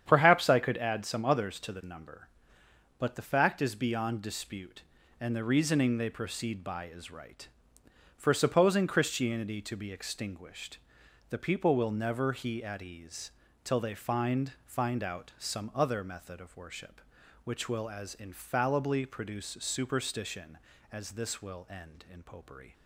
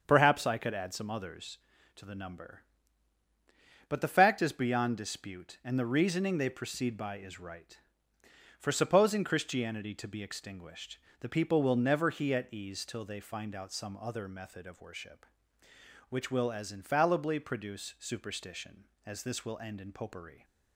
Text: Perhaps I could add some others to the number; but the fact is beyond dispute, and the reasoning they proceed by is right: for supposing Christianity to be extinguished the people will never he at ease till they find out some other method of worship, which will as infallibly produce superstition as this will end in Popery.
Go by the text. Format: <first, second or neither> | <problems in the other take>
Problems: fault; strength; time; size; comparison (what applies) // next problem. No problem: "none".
second | starts louder than the rest; strong; until 1.0 s; 9 dB; also in the second // pauses between "extinguished" and "the"; noticeable; at 10.7 s; 0.50 s long; slight in the second // pauses between "ease" and "till"; slight; at 13.3 s; 0.32 s long // says "find" twice; at 14.6 s